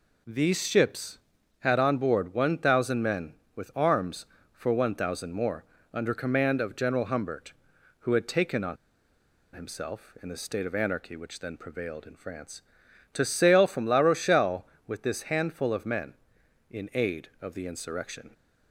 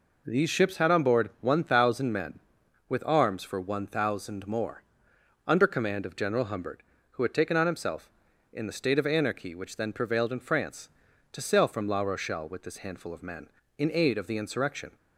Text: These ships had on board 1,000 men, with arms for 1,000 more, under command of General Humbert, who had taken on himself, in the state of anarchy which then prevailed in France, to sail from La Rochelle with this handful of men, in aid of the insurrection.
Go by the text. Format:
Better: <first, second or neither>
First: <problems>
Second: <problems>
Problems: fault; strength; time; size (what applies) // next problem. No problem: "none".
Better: second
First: pauses between "on" and "himself"; noticeable; at 8.7 s; 0.78 s long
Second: none